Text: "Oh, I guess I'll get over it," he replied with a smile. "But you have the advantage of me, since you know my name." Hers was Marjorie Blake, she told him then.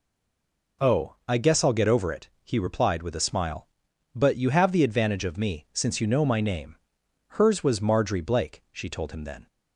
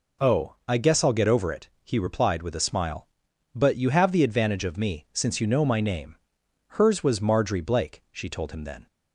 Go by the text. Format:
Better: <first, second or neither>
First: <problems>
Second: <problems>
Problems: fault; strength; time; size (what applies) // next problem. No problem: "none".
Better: second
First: stays silent before the first word; slight; until 0.8 s; 0.8 s long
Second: none